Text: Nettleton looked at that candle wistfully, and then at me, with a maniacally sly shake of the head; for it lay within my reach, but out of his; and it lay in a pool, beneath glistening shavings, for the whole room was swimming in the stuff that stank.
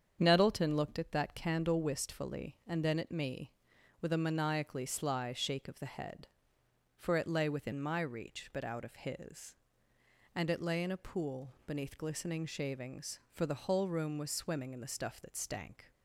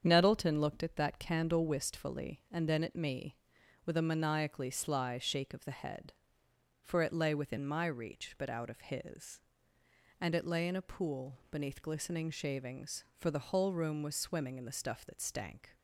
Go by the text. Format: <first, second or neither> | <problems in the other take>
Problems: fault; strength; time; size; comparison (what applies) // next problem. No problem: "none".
neither | starts louder than the rest; strong; the same in both